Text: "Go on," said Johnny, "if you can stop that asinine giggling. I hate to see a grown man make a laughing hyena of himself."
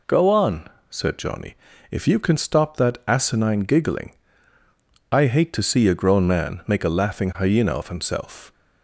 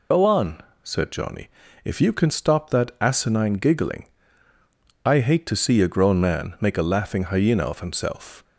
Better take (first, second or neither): first